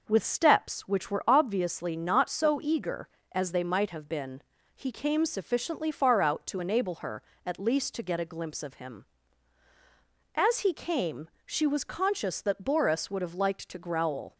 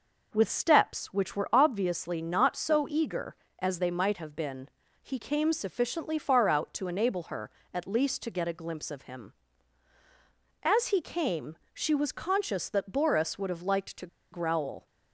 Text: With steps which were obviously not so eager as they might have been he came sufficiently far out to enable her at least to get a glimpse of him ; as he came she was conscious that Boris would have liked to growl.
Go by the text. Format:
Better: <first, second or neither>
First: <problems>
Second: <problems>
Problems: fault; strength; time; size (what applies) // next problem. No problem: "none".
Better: first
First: pauses between "been" and "he"; slight; at 4.4 s; 0.34 s long // pauses between "came" and "she"; slight; at 11.2 s; 0.16 s long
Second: pauses between "been" and "he"; slight; at 4.6 s; 0.34 s long // pauses between "came" and "she"; slight; at 11.5 s; 0.16 s long // pauses between "to" and "growl"; slight; at 14.0 s; 0.25 s long